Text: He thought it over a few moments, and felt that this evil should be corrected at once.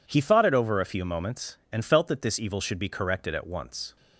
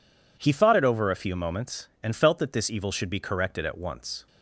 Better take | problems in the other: neither | none

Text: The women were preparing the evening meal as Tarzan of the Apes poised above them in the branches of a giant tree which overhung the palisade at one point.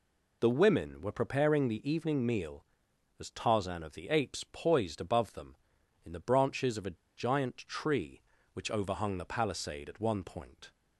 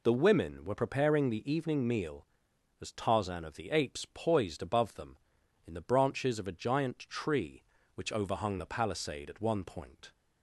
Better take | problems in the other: second | pauses between "a" and "giant"; slight; at 6.9 s; 0.20 s long

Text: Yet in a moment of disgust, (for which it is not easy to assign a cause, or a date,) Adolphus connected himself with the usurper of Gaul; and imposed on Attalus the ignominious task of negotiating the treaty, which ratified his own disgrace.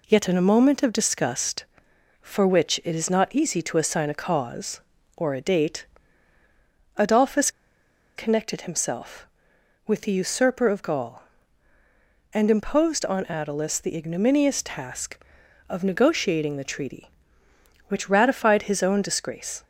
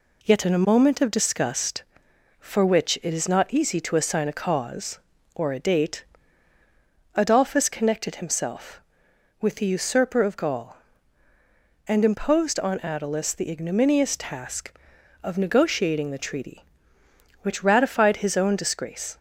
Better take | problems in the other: second | pauses between "Adolphus" and "connected"; noticeable; at 7.4 s; 0.67 s long

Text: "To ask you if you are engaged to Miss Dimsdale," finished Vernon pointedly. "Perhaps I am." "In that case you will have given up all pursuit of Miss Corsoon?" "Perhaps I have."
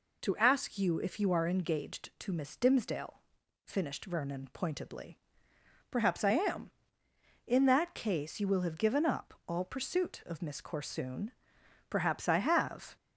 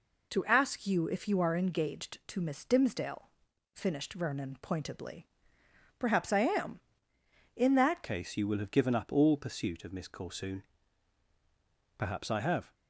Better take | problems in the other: first | changes voice at "case"; from 8.0 s on; 4.7 s long

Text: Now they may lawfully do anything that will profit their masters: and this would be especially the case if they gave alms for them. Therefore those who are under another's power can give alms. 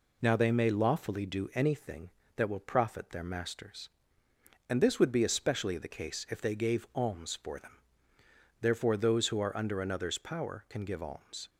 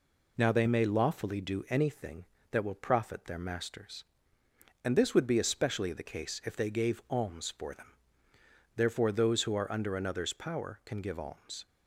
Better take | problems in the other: neither | none

